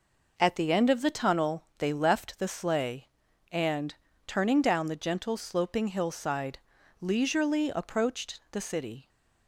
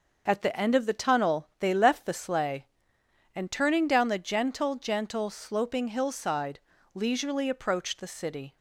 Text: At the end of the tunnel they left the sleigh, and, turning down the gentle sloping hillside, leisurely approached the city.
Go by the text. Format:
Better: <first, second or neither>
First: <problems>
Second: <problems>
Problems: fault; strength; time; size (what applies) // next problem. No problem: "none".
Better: first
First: none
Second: says "gentle" twice; at 4.7 s